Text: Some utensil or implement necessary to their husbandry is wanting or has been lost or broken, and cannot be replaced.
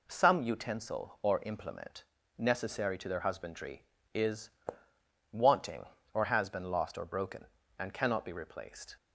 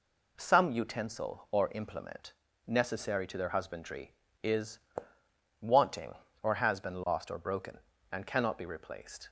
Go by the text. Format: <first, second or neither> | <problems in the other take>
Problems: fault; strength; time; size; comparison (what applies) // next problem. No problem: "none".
neither | pauses between "implement" and "necessary"; slight; the same in both // pauses between "is" and "wanting"; noticeable; the same in both